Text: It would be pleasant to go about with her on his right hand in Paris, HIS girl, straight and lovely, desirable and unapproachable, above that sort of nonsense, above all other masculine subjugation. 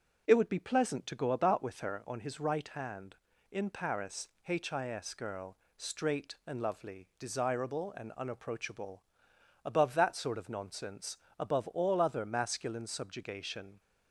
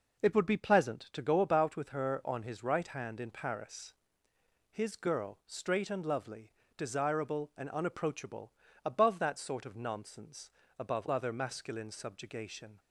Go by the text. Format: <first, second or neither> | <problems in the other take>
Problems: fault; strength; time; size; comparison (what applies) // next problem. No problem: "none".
first | skips "all"; at 11.0 s